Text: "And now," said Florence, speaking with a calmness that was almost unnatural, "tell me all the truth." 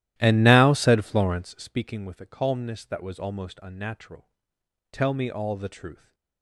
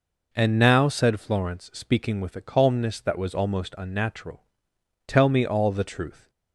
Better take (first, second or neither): second